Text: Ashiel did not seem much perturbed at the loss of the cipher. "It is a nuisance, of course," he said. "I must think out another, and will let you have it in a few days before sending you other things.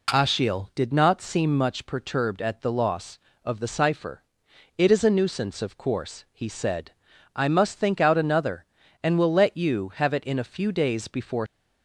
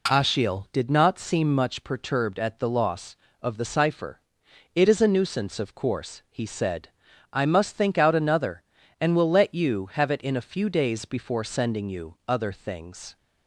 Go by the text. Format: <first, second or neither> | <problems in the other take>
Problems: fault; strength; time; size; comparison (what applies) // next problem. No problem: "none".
second | stops before "sending you other things"; at 11.4 s